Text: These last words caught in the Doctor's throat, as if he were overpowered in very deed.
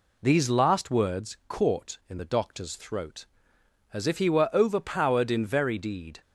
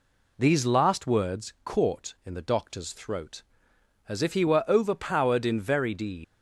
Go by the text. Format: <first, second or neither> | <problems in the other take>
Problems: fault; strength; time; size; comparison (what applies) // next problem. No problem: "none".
first | leaves "deed" unfinished; at 6.2 s; 115 ms